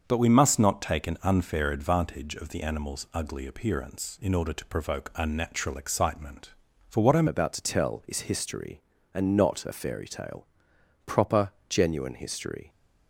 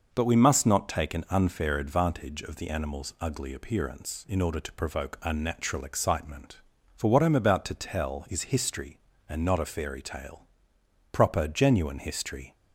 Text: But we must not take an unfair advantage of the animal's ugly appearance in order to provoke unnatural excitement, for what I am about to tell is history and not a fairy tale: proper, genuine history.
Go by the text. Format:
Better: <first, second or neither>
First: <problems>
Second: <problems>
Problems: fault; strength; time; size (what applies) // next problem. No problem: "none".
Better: second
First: starts louder than the rest; until 1.0 s; 6.5 dB // changes voice at "about"; from 7.2 s on; 5.4 s long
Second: none